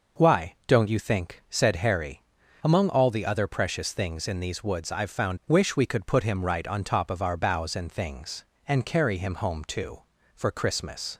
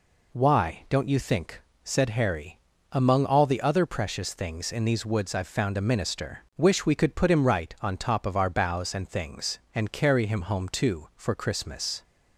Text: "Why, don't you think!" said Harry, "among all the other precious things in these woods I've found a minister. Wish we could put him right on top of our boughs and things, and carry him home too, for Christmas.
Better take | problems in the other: second | skips "a minister"; at 5.4 s

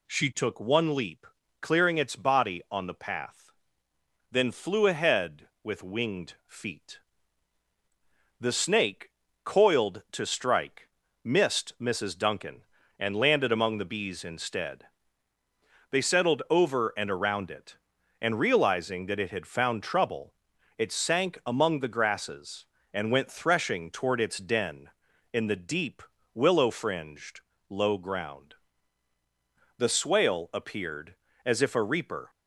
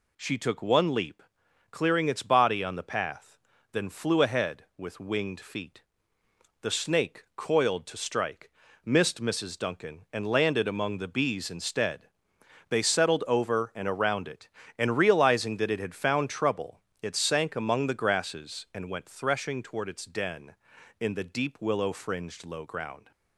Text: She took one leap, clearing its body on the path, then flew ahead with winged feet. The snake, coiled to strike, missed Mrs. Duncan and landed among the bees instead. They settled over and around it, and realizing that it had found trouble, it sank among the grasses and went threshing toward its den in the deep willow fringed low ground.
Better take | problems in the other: second | pauses between "deep" and "willow"; slight; at 26.0 s; 0.32 s long // pauses between "fringed" and "low"; slight; at 27.3 s; 0.30 s long // goes on to say "The swale appeared as if a reaper"; strong; from 29.7 s on; 2.5 s long

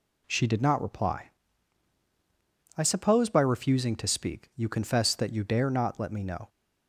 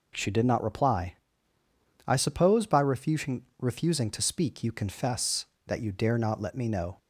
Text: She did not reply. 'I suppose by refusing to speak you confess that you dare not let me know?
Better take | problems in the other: first | says "refusing" twice; at 3.5 s

